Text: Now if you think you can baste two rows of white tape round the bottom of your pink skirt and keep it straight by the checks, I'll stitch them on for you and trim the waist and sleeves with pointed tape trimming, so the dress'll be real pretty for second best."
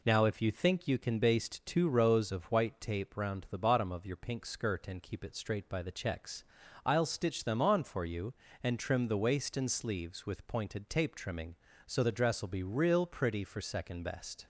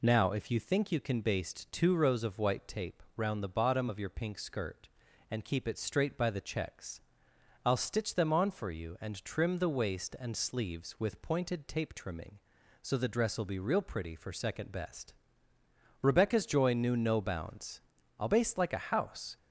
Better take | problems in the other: first | goes on to say "Rebecca's joy knew no bounds I'll baste like a house"; strong; from 16.0 s on; 3.3 s long

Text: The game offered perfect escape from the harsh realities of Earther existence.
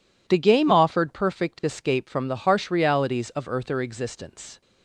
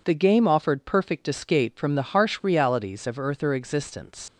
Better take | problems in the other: first | leaves "existence" unfinished; at 4.2 s; 75 ms

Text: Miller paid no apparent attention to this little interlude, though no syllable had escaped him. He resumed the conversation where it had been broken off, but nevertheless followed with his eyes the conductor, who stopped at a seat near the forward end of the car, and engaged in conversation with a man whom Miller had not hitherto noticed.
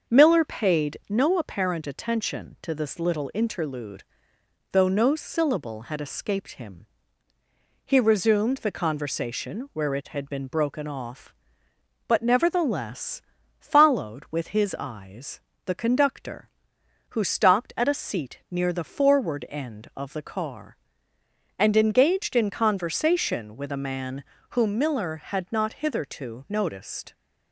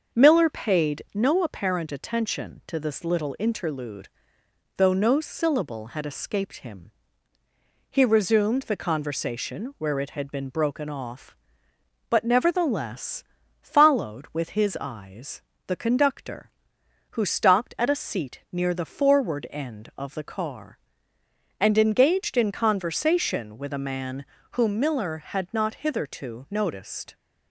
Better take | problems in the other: neither | starts louder than the rest; the same in both // pauses between "nevertheless" and "followed"; the same in both // pauses between "eyes" and "the"; slight; the same in both // pauses between "man" and "whom"; slight; the same in both

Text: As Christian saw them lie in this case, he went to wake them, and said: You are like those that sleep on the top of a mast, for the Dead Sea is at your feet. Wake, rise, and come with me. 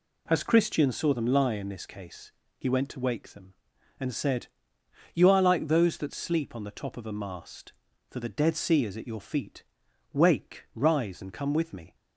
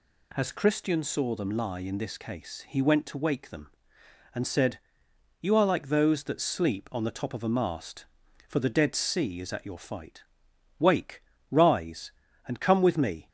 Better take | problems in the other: first | says "fight" for "feet"; at 9.7 s

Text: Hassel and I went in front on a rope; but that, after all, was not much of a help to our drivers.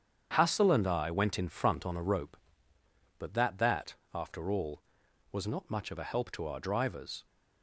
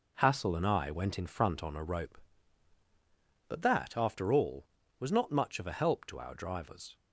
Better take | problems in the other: second | starts louder than the rest; strong; until 1.3 s; 8 dB // says "that" twice; at 3.5 s

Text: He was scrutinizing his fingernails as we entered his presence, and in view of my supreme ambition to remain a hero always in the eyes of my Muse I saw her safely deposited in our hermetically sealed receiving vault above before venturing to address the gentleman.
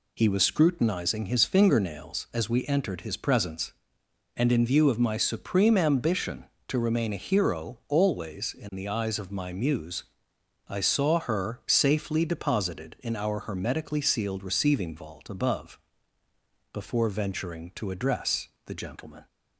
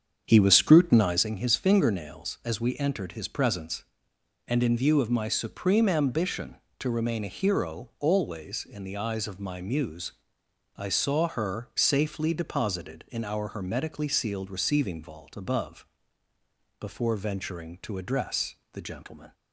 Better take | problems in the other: first | starts louder than the rest; strong; until 1.3 s; 7.5 dB // pauses between "Muse" and "I"; noticeable; at 10.1 s; 0.64 s long; noticeable in the first // pauses between "above" and "before"; noticeable; at 15.8 s; 0.94 s long; noticeable in the first // pauses between "address" and "the"; slight; at 18.5 s; 0.16 s long; slight in the first

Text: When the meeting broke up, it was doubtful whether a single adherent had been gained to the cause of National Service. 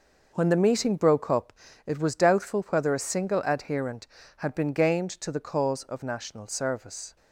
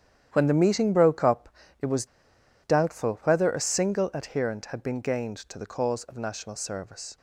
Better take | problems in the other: first | starts louder than the rest; strong; until 1.3 s; 10 dB // pauses between "was" and "doubtful"; noticeable; at 2.0 s; 0.56 s long

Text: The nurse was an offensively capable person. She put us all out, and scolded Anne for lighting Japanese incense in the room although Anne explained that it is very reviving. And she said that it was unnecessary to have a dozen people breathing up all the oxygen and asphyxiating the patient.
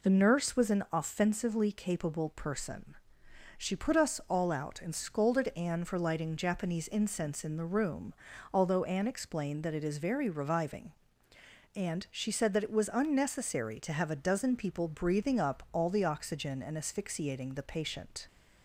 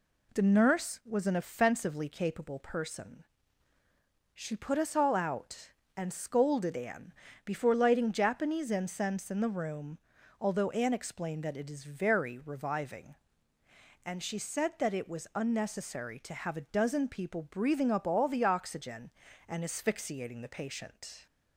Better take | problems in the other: first | says "before" for "for"; at 7.4 s // pauses between "room" and "although"; at 9.9 s; 0.44 s long; also in the first

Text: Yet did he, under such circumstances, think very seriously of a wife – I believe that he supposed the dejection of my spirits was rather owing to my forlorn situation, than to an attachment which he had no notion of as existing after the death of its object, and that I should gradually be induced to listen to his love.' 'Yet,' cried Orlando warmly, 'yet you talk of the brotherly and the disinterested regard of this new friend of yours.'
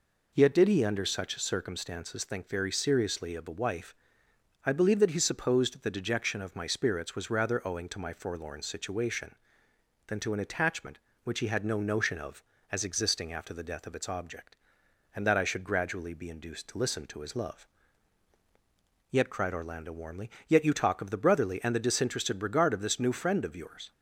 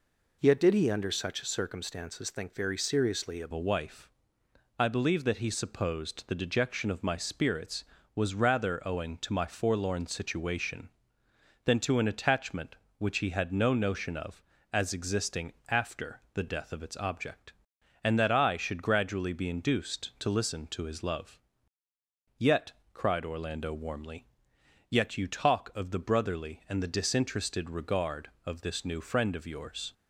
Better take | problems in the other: first | changes voice at "a"; from 3.5 s on; 26.4 s long // pauses between "existing" and "after"; slight; at 15.5 s; 0.16 s long

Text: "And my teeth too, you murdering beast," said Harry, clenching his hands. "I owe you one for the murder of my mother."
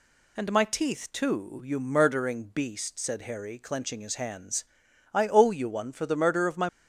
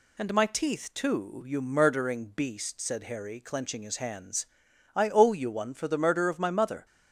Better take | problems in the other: second | stops before "mother"; at 6.6 s

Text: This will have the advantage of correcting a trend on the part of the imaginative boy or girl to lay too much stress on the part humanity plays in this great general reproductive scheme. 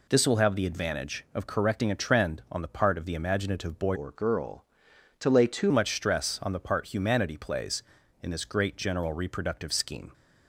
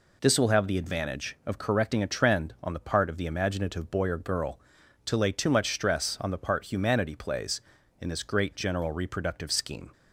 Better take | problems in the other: second | changes voice from "or" to "too"; from 3.9 to 5.7 s; 1.8 s long

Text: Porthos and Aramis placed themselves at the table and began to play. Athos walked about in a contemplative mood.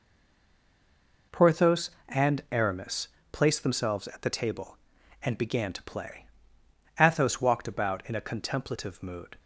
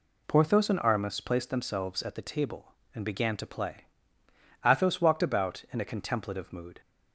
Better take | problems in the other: second | stays silent before the first word; noticeable; until 1.3 s; 1.3 s long // pauses between "Aramis" and "placed"; slight; at 3.0 s; 0.26 s long

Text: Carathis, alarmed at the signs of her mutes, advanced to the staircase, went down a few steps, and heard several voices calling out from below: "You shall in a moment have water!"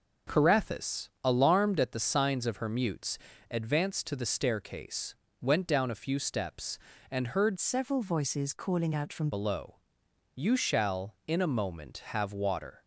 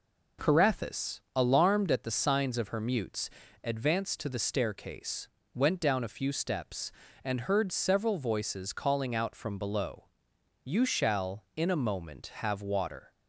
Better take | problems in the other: second | changes voice from "several" to "from"; from 7.5 to 9.2 s; 1.7 s long

